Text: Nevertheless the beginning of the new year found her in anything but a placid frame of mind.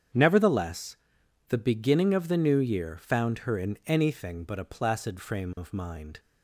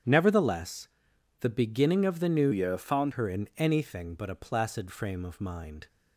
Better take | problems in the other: first | starts louder than the rest; strong; until 1.6 s; 8.5 dB; strong in the first // pauses between "Nevertheless" and "the"; noticeable; at 0.8 s; 0.54 s long; noticeable in the first // changes voice from "year" to "found"; from 2.5 to 3.1 s; 0.6 s long

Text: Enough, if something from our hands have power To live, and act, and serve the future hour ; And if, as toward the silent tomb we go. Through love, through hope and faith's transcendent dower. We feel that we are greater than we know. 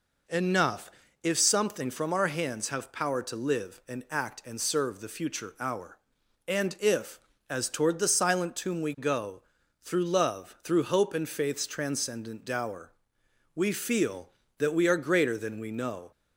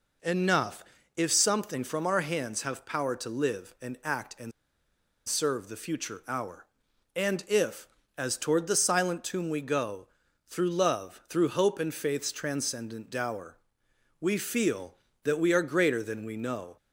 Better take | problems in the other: first | pauses between "and" and "serve"; noticeable; at 4.5 s; 0.76 s long

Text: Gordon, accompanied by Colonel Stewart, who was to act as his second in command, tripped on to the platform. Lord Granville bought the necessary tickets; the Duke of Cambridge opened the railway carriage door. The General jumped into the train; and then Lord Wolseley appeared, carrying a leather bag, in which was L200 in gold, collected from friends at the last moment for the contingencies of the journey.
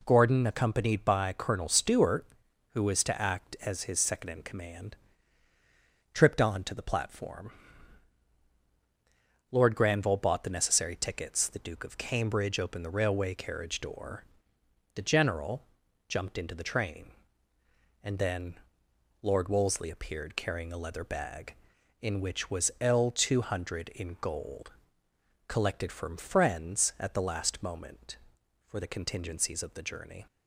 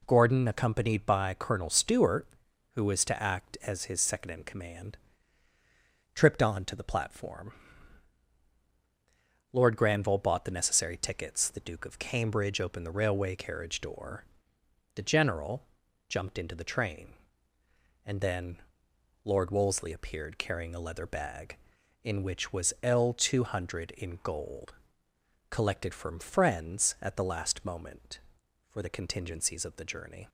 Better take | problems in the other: neither | pauses between "General" and "jumped"; noticeable; the same in both // pauses between "then" and "Lord"; noticeable; the same in both

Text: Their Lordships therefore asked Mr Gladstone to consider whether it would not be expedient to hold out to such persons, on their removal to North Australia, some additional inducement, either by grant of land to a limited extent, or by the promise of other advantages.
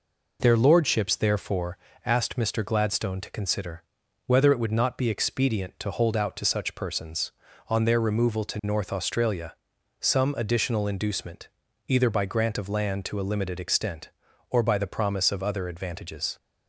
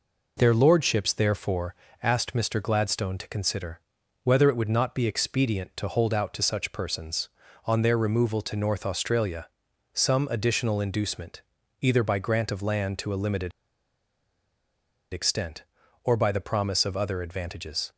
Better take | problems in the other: first | pauses between "therefore" and "asked"; slight; at 1.7 s; 0.26 s long; slight in the first // pauses between "consider" and "whether"; at 3.8 s; 0.42 s long; also in the first // pauses between "limited" and "extent"; strong; at 13.5 s; 1.6 s long

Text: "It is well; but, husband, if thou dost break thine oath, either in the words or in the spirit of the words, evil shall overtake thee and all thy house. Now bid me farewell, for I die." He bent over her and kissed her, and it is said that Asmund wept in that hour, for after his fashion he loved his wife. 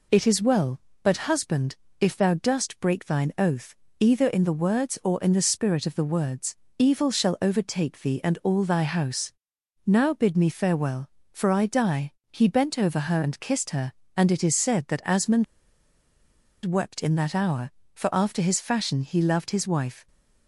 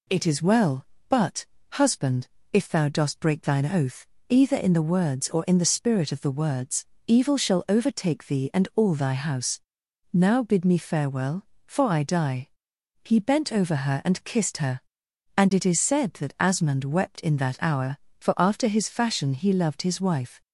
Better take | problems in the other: second | pauses between "Asmund" and "wept"; at 15.4 s; 1.2 s long

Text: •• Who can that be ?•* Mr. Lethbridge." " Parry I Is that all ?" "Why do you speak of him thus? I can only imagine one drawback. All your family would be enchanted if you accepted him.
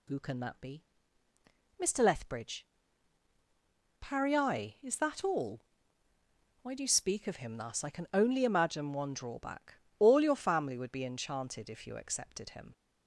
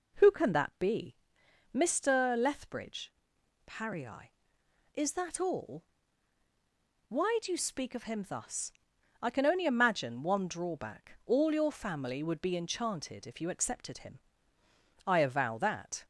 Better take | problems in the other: first | goes on to say "I avow that"; noticeable; from 15.0 s on; 1.0 s long

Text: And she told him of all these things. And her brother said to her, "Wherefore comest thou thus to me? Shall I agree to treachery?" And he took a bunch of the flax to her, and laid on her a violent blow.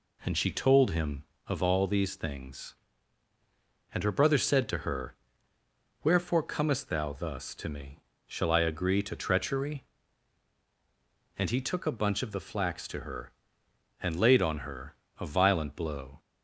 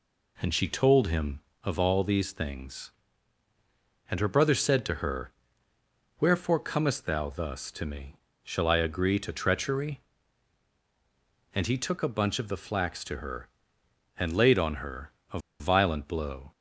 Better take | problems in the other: first | pauses between "her" and "a"; slight; at 15.1 s; 0.22 s long; slight in the first // pauses between "a" and "violent"; slight; at 15.3 s; 0.21 s long

